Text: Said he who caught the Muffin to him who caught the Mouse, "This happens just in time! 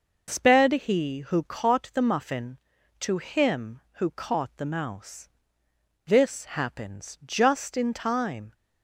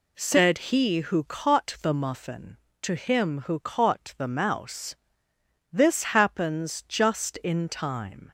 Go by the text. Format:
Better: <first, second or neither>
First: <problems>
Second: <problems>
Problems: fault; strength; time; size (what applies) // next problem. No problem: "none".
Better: second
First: says "Sped" for "Said"; at 0.3 s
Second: none